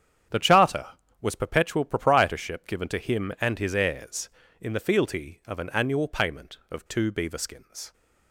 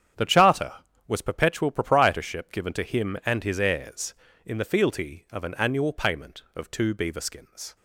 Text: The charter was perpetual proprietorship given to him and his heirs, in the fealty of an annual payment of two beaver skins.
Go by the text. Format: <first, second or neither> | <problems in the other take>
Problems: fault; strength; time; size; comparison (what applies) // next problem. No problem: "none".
neither | starts louder than the rest; strong; the same in both